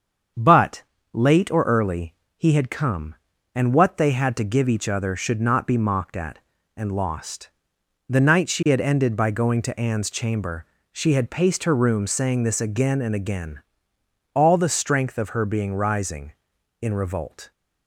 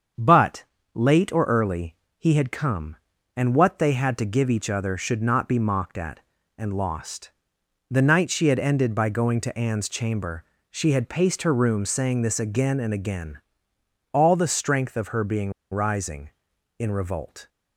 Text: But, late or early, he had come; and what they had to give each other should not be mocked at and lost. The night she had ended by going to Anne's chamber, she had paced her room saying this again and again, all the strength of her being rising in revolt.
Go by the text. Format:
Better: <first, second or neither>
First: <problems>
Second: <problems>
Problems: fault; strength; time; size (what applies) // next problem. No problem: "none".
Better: first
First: starts louder than the rest; strong; until 1.6 s; 7.5 dB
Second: starts louder than the rest; strong; until 1.4 s; 7.5 dB // pauses between "being" and "rising"; slight; at 15.5 s; 0.19 s long